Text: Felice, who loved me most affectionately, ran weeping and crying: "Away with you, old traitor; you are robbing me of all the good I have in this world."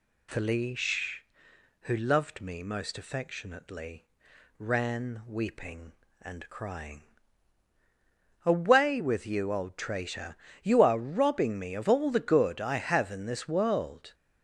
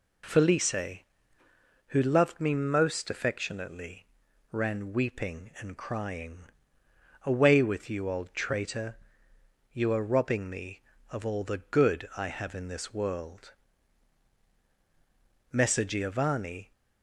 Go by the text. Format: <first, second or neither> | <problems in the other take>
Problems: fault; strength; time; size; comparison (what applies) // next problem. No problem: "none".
first | goes on to say "Messer Giovanni"; noticeable; from 15.5 s on; 1.2 s long